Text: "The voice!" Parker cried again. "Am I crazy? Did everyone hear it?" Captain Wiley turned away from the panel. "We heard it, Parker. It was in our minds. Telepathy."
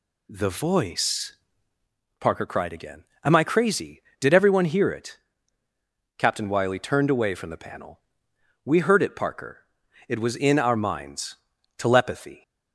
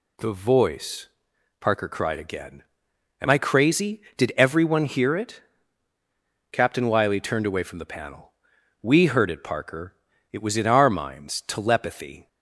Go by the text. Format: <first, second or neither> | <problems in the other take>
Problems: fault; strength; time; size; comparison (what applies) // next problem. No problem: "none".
neither | none